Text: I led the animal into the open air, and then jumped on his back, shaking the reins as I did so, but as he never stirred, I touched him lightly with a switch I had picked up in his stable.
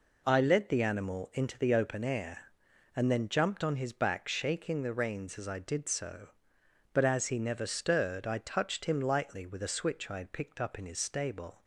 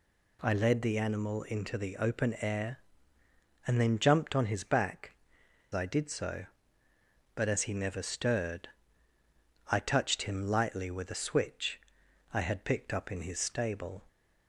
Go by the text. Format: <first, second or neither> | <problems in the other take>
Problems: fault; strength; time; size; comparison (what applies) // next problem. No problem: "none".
first | skips "shaking the reins as"; at 5.4 s // pauses between "switch" and "I"; noticeable; at 11.7 s; 0.54 s long